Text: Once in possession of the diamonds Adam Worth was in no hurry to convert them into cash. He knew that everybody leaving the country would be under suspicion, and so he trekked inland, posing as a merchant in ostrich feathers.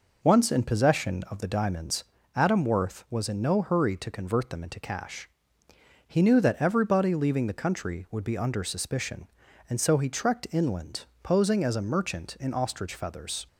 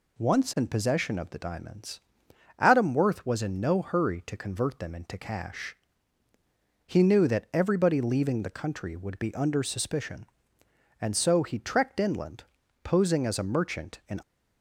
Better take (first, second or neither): first